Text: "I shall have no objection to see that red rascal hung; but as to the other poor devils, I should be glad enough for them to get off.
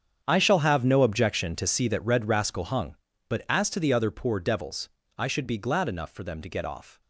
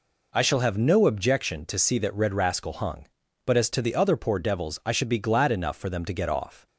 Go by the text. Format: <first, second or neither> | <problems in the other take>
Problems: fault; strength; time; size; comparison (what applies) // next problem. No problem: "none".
second | gets quieter; strong; throughout; 15.5 dB